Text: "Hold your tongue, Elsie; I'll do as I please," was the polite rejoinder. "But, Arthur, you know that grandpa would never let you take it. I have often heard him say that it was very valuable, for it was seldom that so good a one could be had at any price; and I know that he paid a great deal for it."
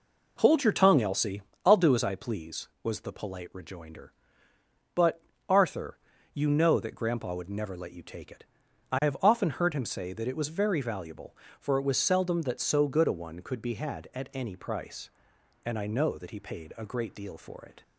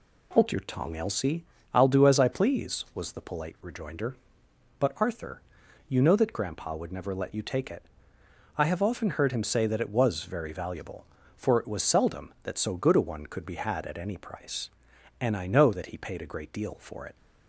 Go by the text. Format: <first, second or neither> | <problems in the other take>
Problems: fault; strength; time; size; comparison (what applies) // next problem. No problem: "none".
neither | none